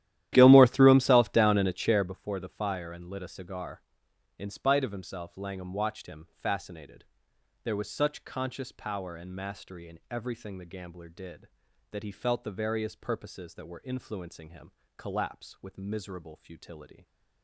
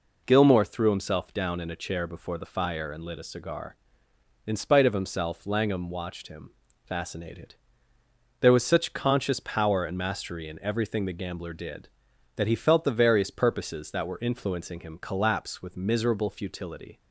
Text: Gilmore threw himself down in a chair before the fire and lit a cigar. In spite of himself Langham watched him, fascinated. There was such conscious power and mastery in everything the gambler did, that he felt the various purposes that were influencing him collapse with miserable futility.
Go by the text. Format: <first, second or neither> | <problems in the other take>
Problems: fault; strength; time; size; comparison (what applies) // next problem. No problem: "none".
second | starts louder than the rest; strong; until 2.2 s; 12.5 dB // pauses between "him" and "collapse"; slight; at 14.7 s; 0.26 s long